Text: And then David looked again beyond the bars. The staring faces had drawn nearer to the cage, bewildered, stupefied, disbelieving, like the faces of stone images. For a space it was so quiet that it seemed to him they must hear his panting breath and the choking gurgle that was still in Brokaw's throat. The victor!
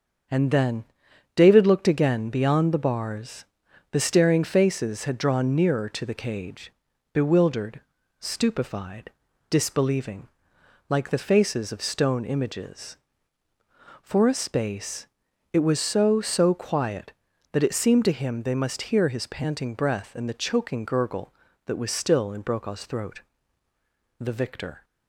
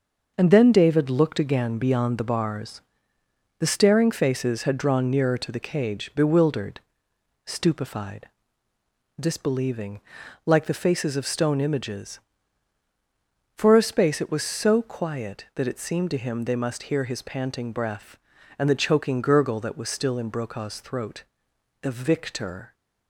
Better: second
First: starts louder than the rest; until 1.8 s; 7 dB // pauses between "then" and "David"; noticeable; at 0.8 s; 0.52 s long // pauses between "space" and "it"; noticeable; at 15.0 s; 0.46 s long // says "so" twice; at 16.2 s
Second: starts louder than the rest; until 1.3 s; 6 dB

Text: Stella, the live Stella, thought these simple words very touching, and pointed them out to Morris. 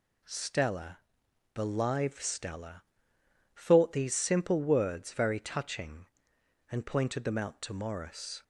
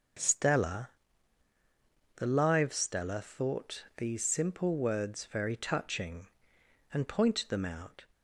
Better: first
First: none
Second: stops before "to Morris"; at 8.1 s

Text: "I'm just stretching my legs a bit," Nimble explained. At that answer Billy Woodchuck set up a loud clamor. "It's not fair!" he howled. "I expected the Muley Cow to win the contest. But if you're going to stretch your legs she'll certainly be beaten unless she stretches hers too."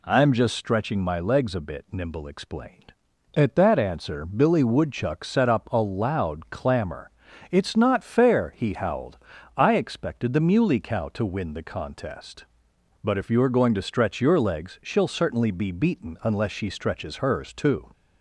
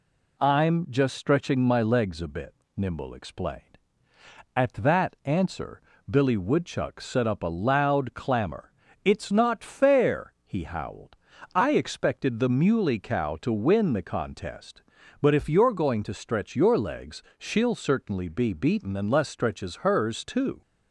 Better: first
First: none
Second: pauses between "answer" and "Billy"; slight; at 5.8 s; 0.30 s long // pauses between "legs" and "she'll"; slight; at 17.2 s; 0.16 s long // skips "she"; at 19.2 s

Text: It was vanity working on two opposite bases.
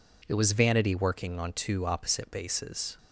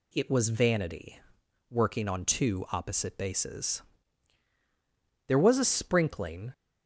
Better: first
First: none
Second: pauses between "vanity" and "working"; noticeable; at 1.1 s; 0.52 s long // goes on to say "There was a sprinkling"; noticeable; from 5.2 s on; 1.2 s long

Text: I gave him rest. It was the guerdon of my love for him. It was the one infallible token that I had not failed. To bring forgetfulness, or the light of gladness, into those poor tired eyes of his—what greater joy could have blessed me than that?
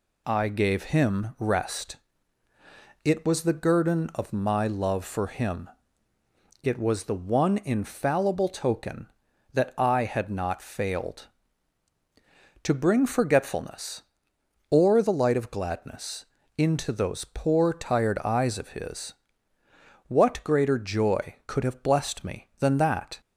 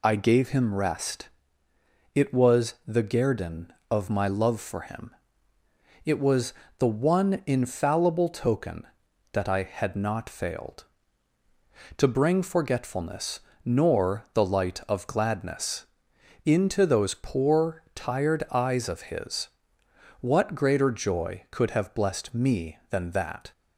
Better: first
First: none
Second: pauses between "was" and "the"; slight; at 6.5 s; 0.24 s long // says "nor" for "or"; at 13.6 s

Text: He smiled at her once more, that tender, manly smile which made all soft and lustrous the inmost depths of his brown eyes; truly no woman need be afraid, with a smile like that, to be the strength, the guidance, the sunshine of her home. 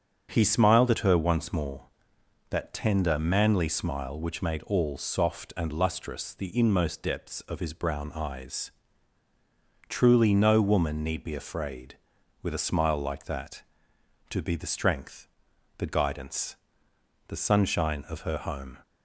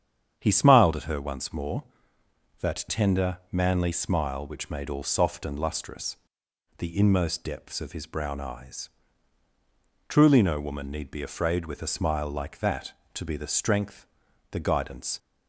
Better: first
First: starts louder than the rest; strong; until 1.3 s; 7 dB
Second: starts louder than the rest; strong; until 1.4 s; 8.5 dB // pauses between "lustrous" and "the"; noticeable; at 6.1 s; 0.62 s long // stops before "the sunshine of her home"; at 15.1 s

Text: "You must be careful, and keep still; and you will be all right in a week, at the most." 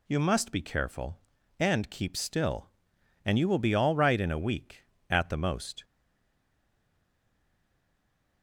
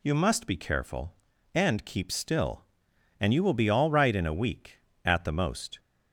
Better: second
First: stays silent after the last word; strong; from 5.8 s on; 2.6 s long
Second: none

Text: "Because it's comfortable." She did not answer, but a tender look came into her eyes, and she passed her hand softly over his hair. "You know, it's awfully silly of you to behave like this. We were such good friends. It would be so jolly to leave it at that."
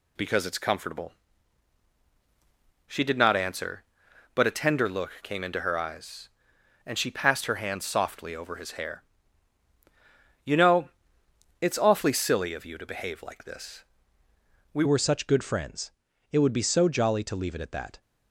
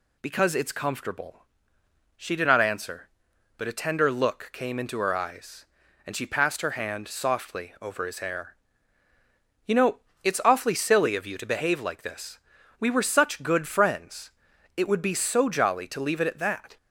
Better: second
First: changes voice at "were"; from 14.8 s on; 3.2 s long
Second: none

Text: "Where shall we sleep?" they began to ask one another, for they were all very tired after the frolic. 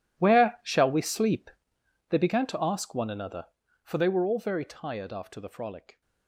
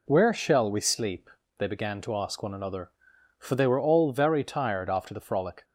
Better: second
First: gets quieter; strong; throughout; 17 dB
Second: none

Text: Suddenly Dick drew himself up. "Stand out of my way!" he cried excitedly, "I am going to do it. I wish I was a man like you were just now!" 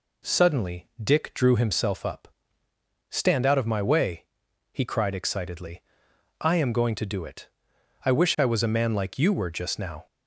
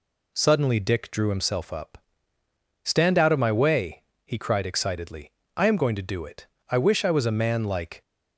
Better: first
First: none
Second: stops before "you were just now"; at 8.0 s

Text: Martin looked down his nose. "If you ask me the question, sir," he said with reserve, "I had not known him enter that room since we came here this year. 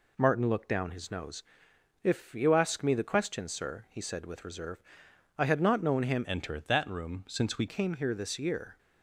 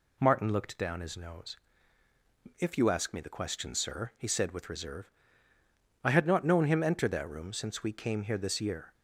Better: second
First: changes voice from "enter" to "we"; from 6.2 to 7.6 s; 1.4 s long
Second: none

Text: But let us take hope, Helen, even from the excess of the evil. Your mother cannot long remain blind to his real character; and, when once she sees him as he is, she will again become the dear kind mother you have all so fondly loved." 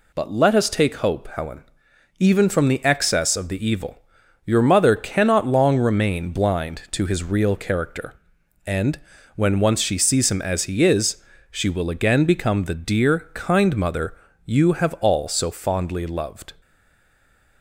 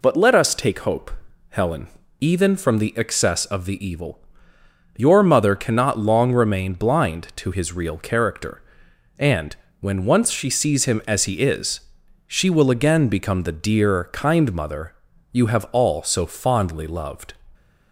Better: second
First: pauses between "mother" and "you"; slight; at 14.1 s; 0.30 s long // stays silent after the last word; from 16.6 s on; 1.0 s long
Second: pauses between "mother" and "you"; at 14.9 s; 0.38 s long

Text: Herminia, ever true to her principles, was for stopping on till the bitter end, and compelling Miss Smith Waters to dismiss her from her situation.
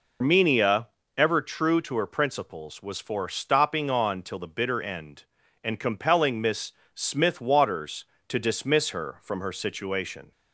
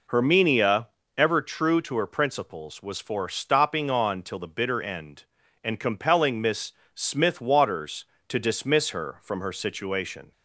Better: second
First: loses the start of "Herminia"; at 0.2 s; 110 ms // pauses between "Miss" and "Smith"; slight; at 6.7 s; 0.20 s long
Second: pauses between "Miss" and "Smith"; slight; at 6.7 s; 0.20 s long

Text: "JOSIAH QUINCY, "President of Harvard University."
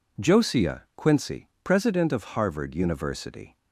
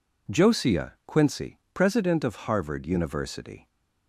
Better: neither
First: none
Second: none

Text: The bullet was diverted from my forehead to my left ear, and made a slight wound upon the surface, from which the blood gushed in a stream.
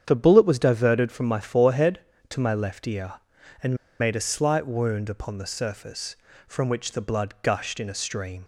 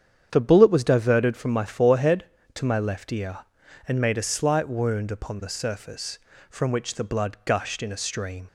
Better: second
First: starts louder than the rest; strong; until 1.0 s; 8.5 dB // pauses between "and" and "made"; slight; at 3.7 s; 0.24 s long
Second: starts louder than the rest; strong; until 1.3 s; 8.5 dB

